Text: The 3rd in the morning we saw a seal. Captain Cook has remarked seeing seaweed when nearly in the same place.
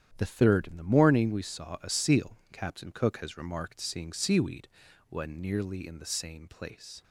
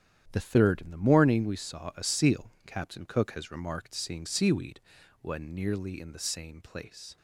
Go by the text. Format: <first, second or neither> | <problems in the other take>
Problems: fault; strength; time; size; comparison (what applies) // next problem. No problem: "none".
neither | starts louder than the rest; strong; the same in both // pauses between "seaweed" and "when"; the same in both